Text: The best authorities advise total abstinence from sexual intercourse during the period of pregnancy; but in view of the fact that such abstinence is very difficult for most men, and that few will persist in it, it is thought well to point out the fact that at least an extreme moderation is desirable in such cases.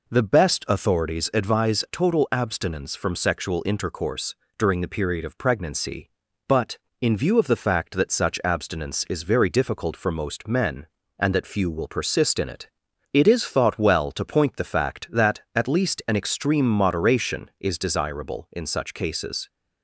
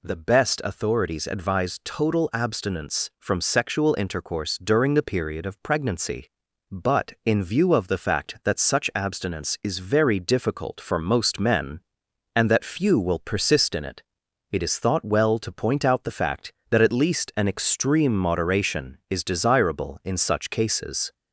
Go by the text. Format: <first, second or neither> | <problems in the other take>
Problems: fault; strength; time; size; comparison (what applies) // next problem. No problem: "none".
second | pauses between "intercourse" and "during"; slight; at 4.3 s; 0.20 s long // skips "out"; at 14.5 s